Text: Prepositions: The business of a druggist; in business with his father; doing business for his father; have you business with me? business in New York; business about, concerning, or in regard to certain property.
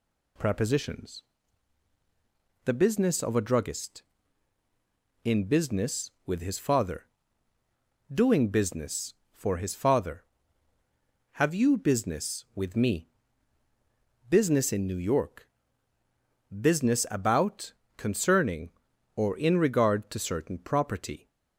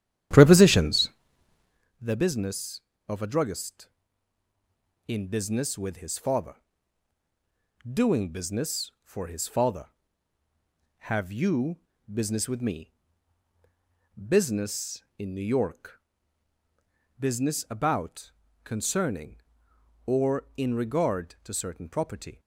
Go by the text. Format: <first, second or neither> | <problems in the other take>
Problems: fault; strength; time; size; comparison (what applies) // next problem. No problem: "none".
first | starts louder than the rest; strong; until 1.9 s; 10.5 dB // pauses between "you" and "business"; slight; at 11.7 s; 0.32 s long